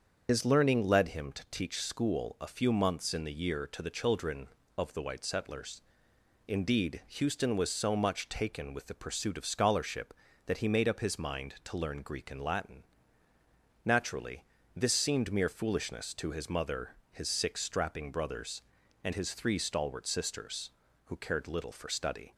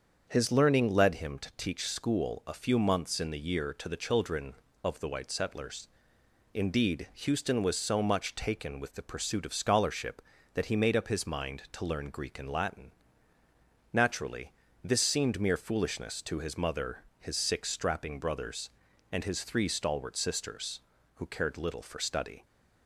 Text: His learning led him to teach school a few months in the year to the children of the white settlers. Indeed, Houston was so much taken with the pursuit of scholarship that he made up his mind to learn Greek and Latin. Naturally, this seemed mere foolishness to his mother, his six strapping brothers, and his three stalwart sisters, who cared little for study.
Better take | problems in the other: second | loses the start of "His"; at 0.2 s; 60 ms // starts louder than the rest; until 1.3 s; 7 dB; also in the second

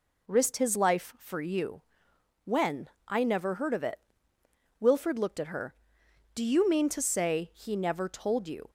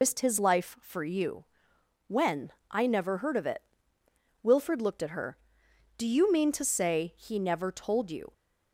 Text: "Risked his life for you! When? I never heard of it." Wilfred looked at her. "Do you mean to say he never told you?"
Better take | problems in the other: first | loses the start of "Risked"; at 0.0 s; 105 ms

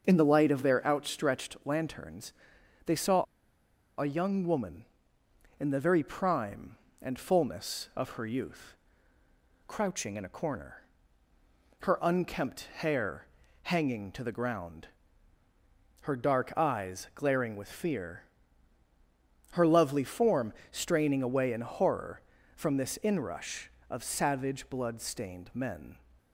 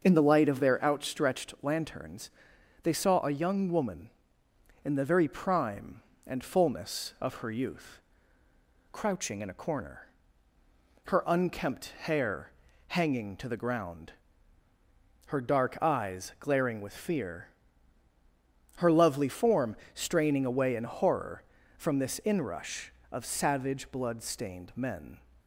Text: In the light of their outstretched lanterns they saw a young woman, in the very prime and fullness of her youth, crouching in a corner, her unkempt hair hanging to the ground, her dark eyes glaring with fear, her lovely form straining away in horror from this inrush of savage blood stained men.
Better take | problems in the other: second | starts louder than the rest; until 1.0 s; 6 dB; also in the second // pauses between "lanterns" and "they"; noticeable; at 2.3 s; 0.54 s long; noticeable in the second // pauses between "saw" and "a"; noticeable; at 3.2 s; 0.75 s long // pauses between "hair" and "hanging"; at 13.2 s; 0.38 s long; also in the second // pauses between "form" and "straining"; slight; at 20.5 s; 0.18 s long; slight in the second

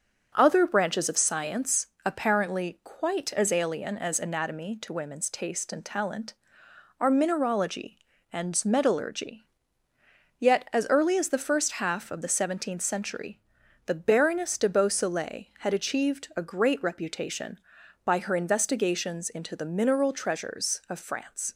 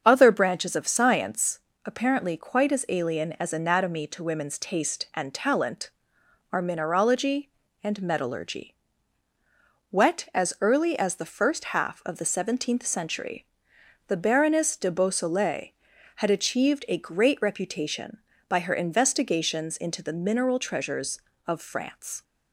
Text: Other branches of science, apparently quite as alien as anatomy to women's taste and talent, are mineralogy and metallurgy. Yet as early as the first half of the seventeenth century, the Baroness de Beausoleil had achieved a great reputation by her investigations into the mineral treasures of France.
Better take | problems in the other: first | starts louder than the rest; until 1.0 s; 7 dB; noticeable in the first // says "Wet" for "Yet"; at 9.9 s

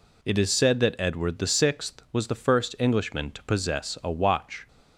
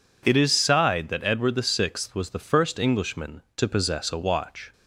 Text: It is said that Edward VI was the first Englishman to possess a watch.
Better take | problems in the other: first | says "sighed" for "said"; at 0.5 s

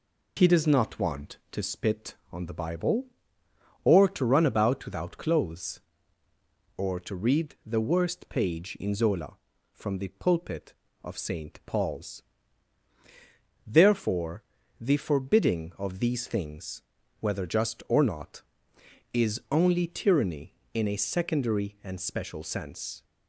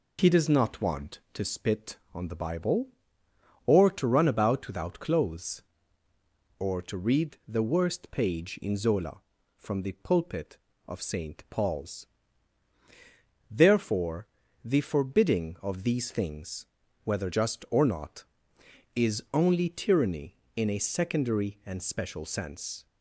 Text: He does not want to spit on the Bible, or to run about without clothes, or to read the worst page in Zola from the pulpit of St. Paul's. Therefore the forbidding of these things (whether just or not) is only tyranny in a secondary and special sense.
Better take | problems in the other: neither | pauses between "Therefore" and "the"; slight; the same in both

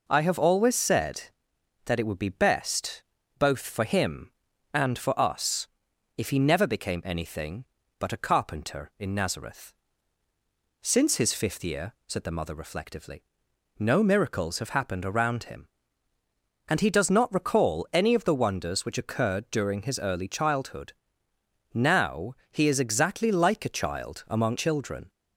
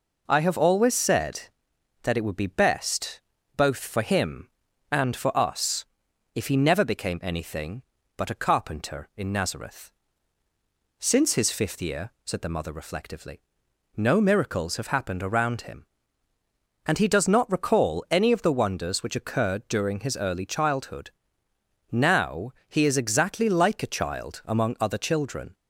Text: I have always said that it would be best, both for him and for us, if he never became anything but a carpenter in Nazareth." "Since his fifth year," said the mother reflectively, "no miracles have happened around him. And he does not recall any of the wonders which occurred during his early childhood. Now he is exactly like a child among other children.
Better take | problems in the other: second | pauses between "Now" and "he"; slight; at 22.3 s; 0.16 s long; slight in the second // skips "other"; at 24.5 s

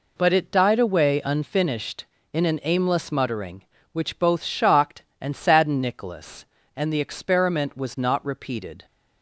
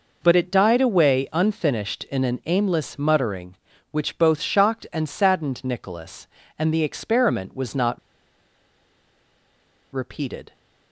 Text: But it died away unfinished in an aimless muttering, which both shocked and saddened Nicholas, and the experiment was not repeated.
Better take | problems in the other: first | pauses between "not" and "repeated"; strong; at 7.9 s; 1.9 s long

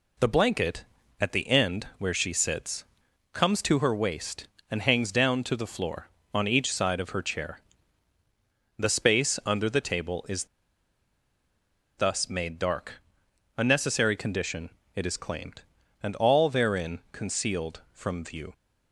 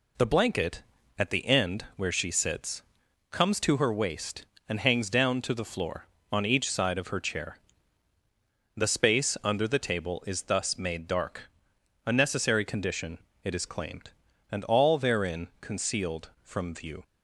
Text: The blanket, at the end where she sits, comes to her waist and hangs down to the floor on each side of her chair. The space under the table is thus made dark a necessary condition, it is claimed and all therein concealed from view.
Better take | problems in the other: second | pauses between "is" and "thus"; strong; at 10.4 s; 1.5 s long // pauses between "dark" and "a"; noticeable; at 12.9 s; 0.64 s long; noticeable in the second

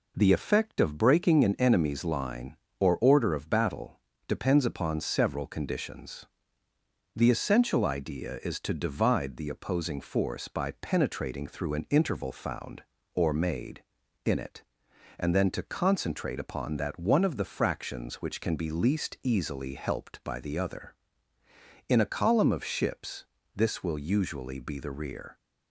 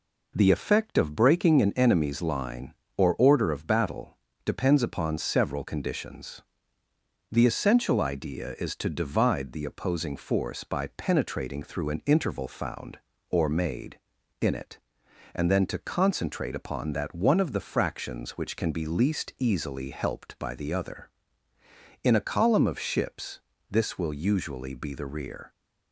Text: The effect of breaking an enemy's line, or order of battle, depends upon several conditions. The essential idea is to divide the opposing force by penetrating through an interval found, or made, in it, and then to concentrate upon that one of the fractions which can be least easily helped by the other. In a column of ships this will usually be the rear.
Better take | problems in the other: neither | pauses between "ships" and "this"; slight; the same in both

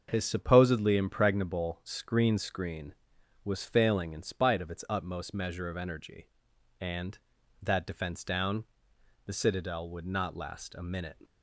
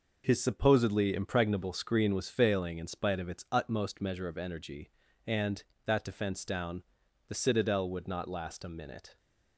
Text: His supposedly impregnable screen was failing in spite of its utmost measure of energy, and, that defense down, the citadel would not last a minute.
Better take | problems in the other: second | starts louder than the rest; until 1.1 s; 6.5 dB // says "screen" twice; at 2.3 s

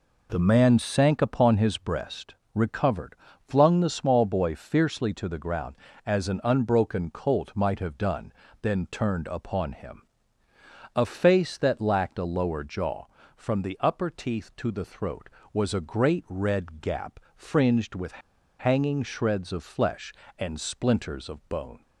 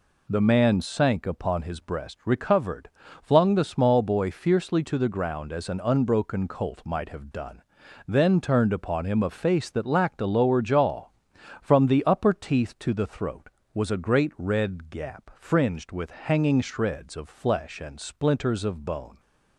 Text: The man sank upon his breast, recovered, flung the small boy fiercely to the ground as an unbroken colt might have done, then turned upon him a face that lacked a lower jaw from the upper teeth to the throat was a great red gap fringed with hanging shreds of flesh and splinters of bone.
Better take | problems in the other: second | pauses between "him" and "a"; noticeable; at 10.0 s; 0.92 s long // pauses between "gap" and "fringed"; slight; at 17.1 s; 0.16 s long // pauses between "with" and "hanging"; at 18.2 s; 0.39 s long

